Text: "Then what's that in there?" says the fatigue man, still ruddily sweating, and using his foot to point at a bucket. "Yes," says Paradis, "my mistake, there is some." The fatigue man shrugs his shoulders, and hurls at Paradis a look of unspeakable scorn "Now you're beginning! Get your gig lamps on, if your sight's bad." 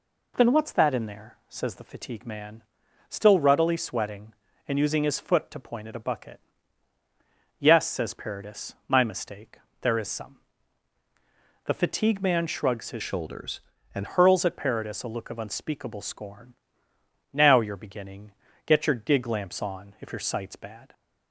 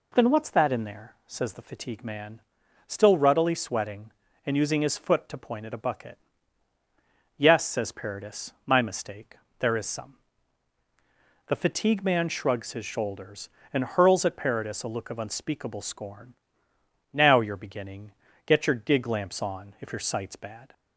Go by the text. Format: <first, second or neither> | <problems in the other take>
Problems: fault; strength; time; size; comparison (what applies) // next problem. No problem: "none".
second | changes voice from "shoulders" to "and"; from 13.0 to 14.0 s; 1.0 s long // pauses between "scorn" and "Now"; noticeable; at 16.5 s; 0.80 s long; noticeable in the second